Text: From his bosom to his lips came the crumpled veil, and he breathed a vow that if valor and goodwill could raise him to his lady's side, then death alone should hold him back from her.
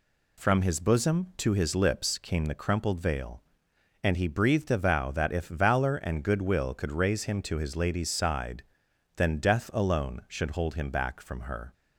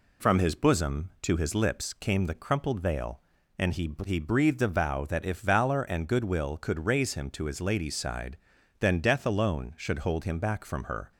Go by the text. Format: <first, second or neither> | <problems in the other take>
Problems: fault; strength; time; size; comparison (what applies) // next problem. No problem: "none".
first | says "he" twice; at 4.0 s